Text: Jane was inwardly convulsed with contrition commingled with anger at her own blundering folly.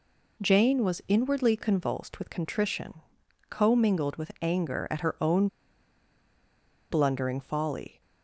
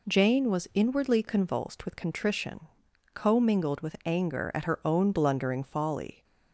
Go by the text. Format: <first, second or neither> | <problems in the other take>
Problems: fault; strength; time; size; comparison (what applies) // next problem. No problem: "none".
second | pauses between "contrition" and "commingled"; noticeable; at 2.9 s; 0.50 s long; noticeable in the second // pauses between "own" and "blundering"; strong; at 5.4 s; 1.4 s long